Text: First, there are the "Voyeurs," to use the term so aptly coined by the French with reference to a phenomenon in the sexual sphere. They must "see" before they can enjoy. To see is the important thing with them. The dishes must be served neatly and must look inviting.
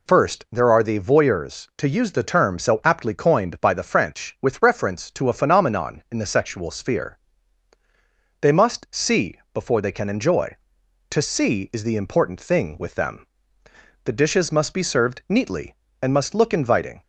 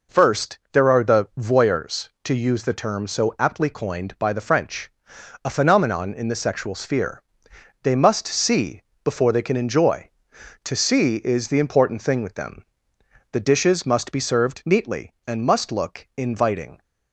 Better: first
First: none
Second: skips "with reference to"; at 5.1 s // pauses between "see" and "before"; slight; at 8.8 s; 0.22 s long

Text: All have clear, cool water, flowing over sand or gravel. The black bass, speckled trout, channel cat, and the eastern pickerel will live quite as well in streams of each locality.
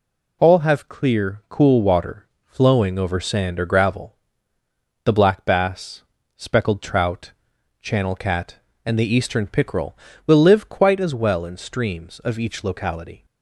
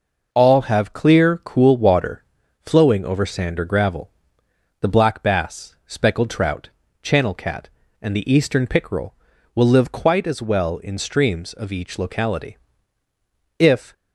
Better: first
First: none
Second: goes on to say "If"; slight; from 13.5 s on; 0.34 s long

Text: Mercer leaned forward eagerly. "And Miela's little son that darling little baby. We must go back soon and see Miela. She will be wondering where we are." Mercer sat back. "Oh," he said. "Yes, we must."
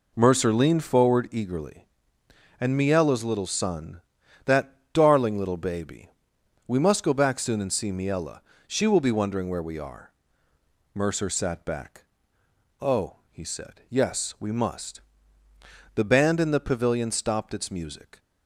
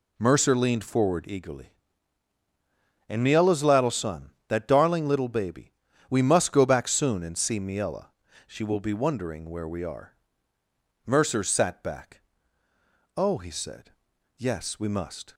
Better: second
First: pauses between "that" and "darling"; slight; at 4.7 s; 0.18 s long // goes on to say "The band in the pavilion stopped its music"; strong; from 15.9 s on; 2.2 s long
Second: none

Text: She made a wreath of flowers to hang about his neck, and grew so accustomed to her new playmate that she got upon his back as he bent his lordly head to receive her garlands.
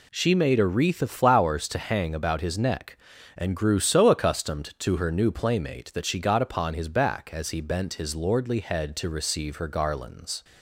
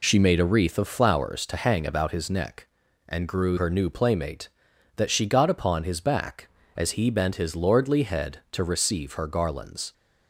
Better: first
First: none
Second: skips "so accustomed to"; at 3.5 s

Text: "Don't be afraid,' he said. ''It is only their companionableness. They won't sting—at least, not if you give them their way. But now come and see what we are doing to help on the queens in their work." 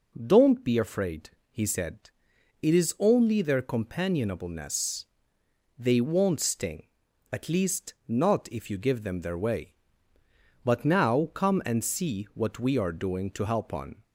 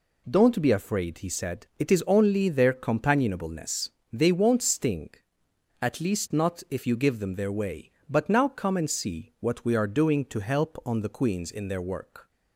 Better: second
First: stops before "the queens in their work"; at 14.0 s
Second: none

